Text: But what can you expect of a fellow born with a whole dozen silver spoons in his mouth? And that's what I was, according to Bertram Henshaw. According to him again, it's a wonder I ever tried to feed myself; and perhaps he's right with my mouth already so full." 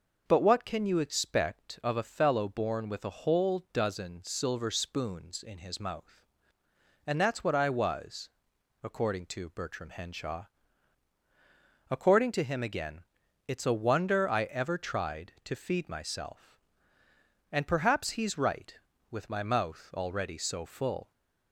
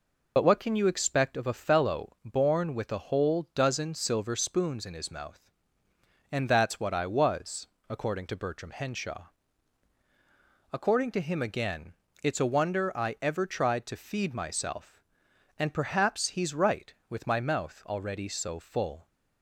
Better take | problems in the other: first | loses the start of "But"; at 0.3 s; 50 ms

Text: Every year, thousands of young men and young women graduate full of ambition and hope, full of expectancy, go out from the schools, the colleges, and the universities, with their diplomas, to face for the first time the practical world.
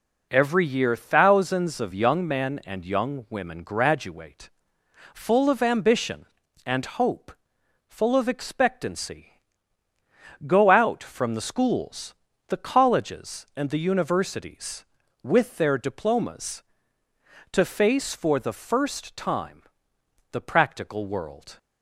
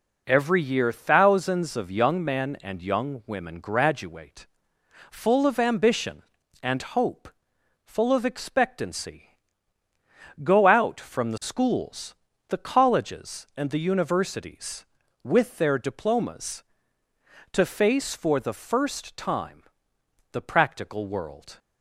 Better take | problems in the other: neither | pauses between "graduate" and "full"; noticeable; the same in both // pauses between "time" and "the"; noticeable; the same in both

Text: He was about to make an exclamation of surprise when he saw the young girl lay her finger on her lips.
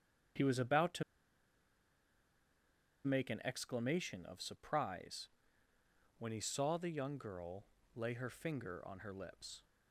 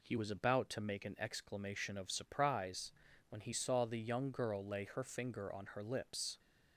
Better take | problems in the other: second | starts louder than the rest; strong; until 3.4 s; 7.5 dB // pauses between "to" and "make"; strong; at 1.0 s; 2.0 s long // pauses between "surprise" and "when"; noticeable; at 5.2 s; 0.92 s long; also in the second // pauses between "girl" and "lay"; slight; at 7.6 s; 0.30 s long

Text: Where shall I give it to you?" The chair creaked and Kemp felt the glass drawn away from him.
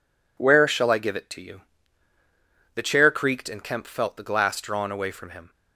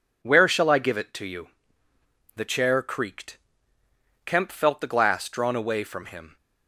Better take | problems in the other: first | skips "and"; at 3.8 s

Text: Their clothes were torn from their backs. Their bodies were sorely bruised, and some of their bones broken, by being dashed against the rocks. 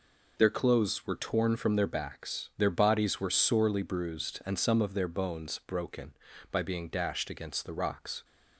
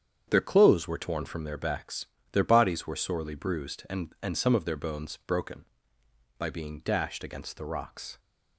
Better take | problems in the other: first | starts louder than the rest; strong; until 1.2 s; 8 dB // says "and" twice; at 4.2 s

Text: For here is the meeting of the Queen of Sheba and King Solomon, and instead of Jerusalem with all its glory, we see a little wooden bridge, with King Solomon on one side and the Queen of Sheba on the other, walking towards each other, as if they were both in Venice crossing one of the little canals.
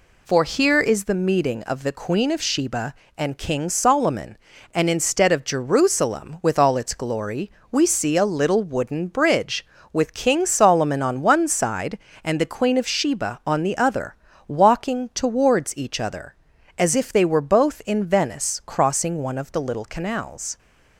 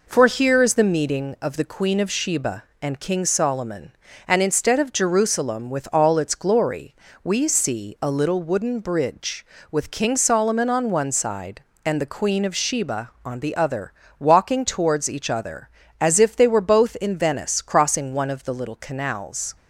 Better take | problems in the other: neither | none

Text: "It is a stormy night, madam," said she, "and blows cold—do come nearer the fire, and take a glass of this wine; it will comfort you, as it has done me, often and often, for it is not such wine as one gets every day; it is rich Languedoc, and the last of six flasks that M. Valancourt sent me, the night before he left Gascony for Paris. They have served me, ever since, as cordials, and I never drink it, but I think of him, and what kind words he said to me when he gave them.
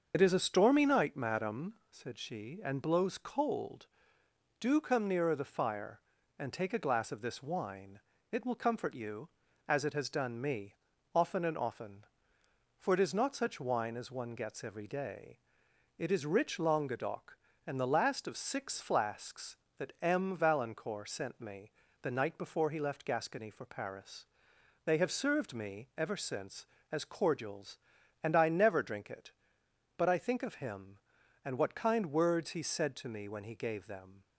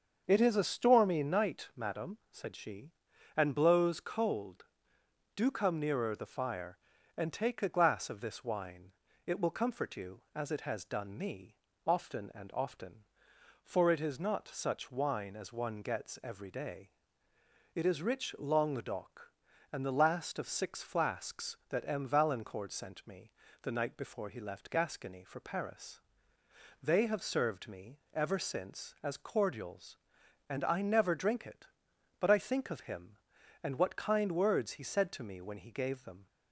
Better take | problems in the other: second | loses the start of "It"; at 0.1 s; 60 ms // starts louder than the rest; until 1.1 s; 6.5 dB; also in the second

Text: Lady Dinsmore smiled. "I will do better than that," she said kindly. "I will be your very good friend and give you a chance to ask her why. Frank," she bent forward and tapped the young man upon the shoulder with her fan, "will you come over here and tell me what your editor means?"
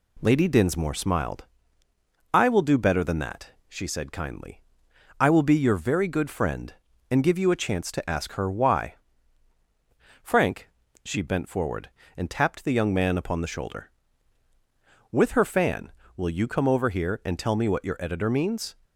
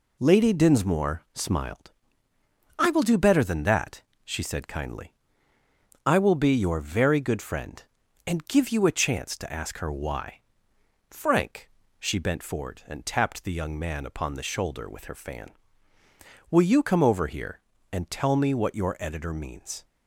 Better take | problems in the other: neither | none

